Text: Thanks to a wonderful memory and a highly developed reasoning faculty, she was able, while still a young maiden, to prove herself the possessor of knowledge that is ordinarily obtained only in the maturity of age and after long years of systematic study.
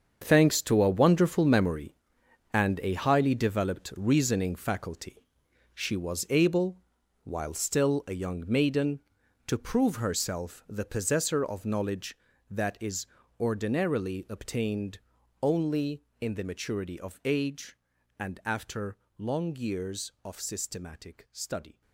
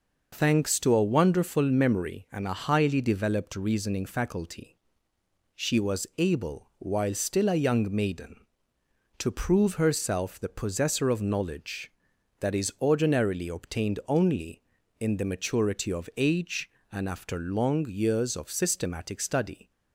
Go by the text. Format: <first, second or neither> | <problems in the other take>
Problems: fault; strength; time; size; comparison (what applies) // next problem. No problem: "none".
second | gets quieter; strong; throughout; 12.5 dB // pauses between "is" and "ordinarily"; slight; at 13.0 s; 0.32 s long // pauses between "obtained" and "only"; at 14.9 s; 0.42 s long // pauses between "after" and "long"; slight; at 18.9 s; 0.20 s long